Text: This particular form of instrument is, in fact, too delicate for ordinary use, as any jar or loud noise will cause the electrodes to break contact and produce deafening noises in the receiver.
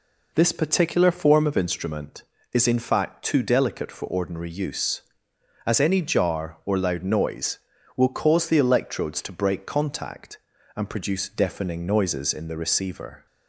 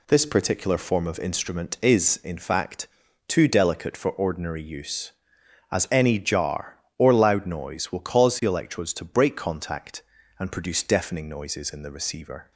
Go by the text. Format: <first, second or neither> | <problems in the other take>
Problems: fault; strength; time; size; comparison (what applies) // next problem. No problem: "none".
neither | none